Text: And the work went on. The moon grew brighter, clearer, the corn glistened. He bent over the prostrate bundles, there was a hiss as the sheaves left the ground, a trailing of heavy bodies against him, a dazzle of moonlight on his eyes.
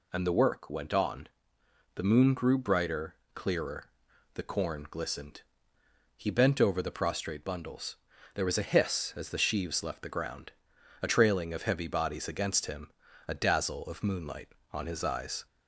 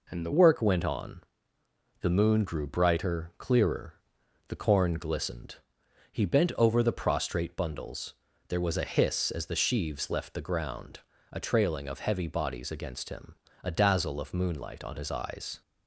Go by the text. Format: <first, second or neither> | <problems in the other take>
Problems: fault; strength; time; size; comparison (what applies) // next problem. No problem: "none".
first | changes voice at "work"; from 0.3 s on; 15.3 s long